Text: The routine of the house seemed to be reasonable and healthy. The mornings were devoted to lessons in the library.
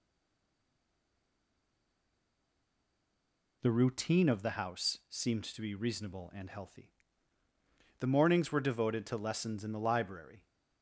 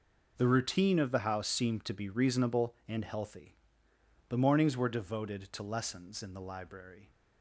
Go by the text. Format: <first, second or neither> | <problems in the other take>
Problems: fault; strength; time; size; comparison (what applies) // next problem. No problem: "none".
second | stays silent before the first word; strong; until 3.6 s; 3.6 s long